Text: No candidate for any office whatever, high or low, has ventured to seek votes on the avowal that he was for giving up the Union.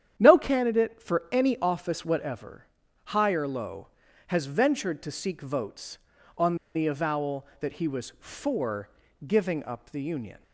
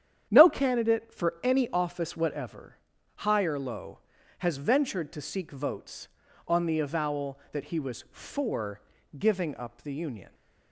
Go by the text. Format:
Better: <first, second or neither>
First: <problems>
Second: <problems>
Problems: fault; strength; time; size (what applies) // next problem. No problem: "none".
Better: second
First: starts louder than the rest; strong; until 1.1 s; 9.5 dB // pauses between "on" and "the"; slight; at 6.5 s; 0.20 s long // pauses between "for" and "giving"; at 8.8 s; 0.38 s long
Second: starts louder than the rest; strong; until 1.3 s; 9.5 dB // pauses between "for" and "giving"; at 8.7 s; 0.38 s long